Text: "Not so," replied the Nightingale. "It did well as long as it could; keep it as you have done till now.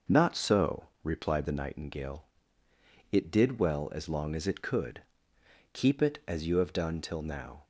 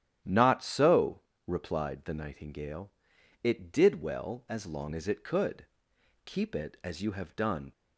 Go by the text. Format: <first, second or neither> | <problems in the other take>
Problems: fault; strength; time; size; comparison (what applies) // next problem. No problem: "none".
first | starts louder than the rest; strong; until 1.5 s; 11 dB // stops before "till now"; at 7.7 s